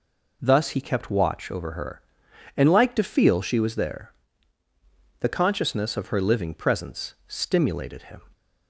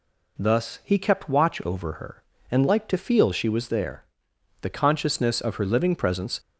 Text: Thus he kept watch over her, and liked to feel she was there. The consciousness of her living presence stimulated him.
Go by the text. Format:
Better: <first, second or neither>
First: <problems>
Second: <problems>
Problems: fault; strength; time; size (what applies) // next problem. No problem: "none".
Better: first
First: none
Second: stops before "stimulated him"; at 6.3 s